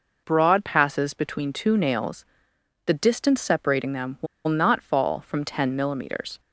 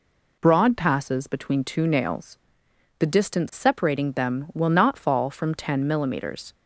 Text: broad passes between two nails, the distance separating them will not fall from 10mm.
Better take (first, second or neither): second